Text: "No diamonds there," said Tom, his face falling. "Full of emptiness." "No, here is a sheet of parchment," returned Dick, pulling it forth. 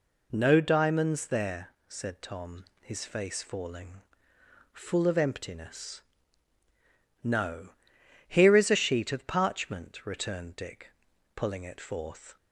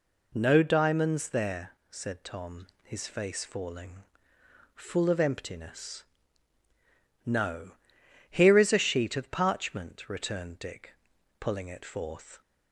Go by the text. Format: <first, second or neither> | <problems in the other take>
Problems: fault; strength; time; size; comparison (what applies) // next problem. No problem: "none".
neither | none